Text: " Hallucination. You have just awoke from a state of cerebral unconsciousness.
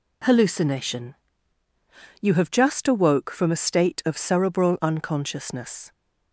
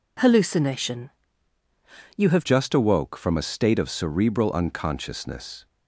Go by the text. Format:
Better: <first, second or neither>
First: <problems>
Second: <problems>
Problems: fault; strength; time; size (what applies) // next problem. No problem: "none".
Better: first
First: none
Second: changes voice at "just"; from 2.4 s on; 3.2 s long